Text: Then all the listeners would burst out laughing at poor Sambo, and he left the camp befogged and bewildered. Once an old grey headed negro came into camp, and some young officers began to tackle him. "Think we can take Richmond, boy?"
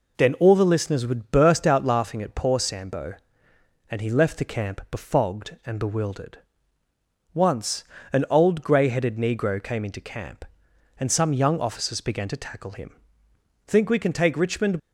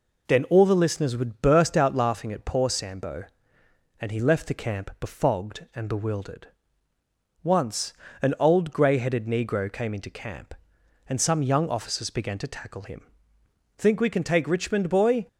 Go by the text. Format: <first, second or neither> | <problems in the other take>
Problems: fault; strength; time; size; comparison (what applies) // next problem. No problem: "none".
second | pauses between "Once" and "an"; slight; at 7.8 s; 0.28 s long; slight in the second // stops before "boy"; at 14.7 s